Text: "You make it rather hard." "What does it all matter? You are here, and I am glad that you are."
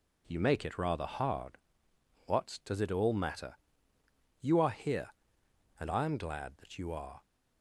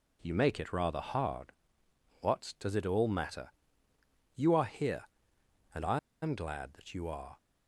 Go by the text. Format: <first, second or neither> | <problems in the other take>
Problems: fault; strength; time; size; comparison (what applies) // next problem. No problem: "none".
first | pauses between "I" and "am"; slight; at 5.9 s; 0.23 s long